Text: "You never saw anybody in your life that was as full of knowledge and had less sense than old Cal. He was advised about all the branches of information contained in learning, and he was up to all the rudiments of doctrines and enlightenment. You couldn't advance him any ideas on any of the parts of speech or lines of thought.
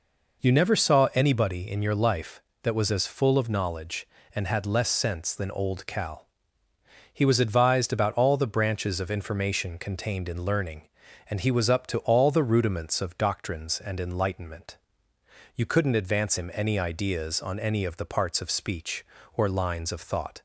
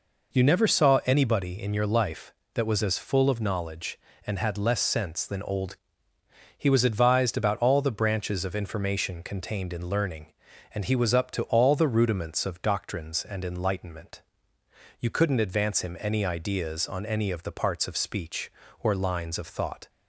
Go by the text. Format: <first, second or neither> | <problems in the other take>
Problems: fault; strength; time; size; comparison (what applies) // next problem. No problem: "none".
first | skips "Cal"; at 6.1 s